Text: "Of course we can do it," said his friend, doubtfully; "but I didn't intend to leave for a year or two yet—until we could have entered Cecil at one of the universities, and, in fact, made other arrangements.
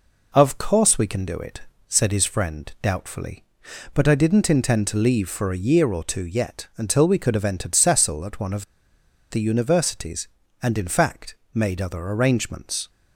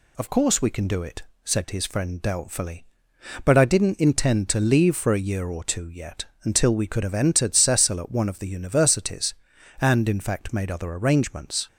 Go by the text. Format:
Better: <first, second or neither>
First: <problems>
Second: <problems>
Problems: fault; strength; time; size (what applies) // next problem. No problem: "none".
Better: second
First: pauses between "of" and "the"; noticeable; at 8.6 s; 0.65 s long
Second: none